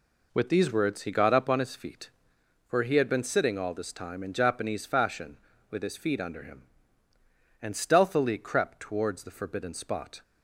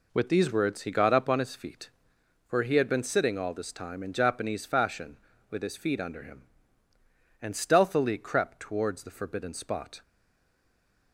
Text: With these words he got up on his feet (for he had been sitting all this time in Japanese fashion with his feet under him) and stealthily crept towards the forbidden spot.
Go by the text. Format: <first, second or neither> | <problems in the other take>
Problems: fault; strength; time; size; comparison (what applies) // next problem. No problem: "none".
first | stays silent after the last word; from 10.0 s on; 1.1 s long